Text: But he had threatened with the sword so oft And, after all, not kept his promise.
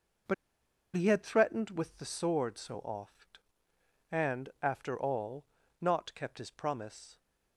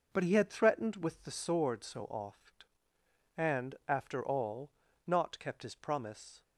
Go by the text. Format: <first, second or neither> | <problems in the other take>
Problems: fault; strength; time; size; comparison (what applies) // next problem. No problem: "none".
second | pauses between "But" and "he"; noticeable; at 0.3 s; 0.61 s long